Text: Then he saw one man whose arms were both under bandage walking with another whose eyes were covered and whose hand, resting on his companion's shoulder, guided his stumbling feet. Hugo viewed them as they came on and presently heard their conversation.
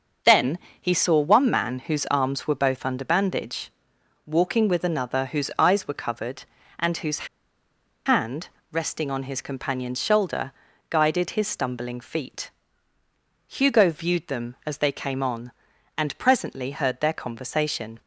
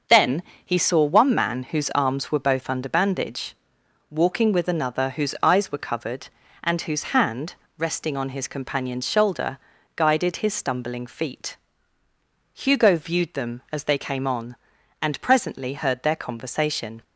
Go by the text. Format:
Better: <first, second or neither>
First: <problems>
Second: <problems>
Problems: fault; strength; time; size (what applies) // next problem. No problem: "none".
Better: second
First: starts louder than the rest; until 1.4 s; 6.5 dB // pauses between "Then" and "he"; slight; at 0.5 s; 0.22 s long // pauses between "bandage" and "walking"; noticeable; at 3.7 s; 0.56 s long // pauses between "whose" and "hand"; noticeable; at 7.2 s; 0.80 s long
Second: starts louder than the rest; until 1.3 s; 6.5 dB // pauses between "Then" and "he"; slight; at 0.4 s; 0.22 s long // pauses between "bandage" and "walking"; noticeable; at 3.5 s; 0.56 s long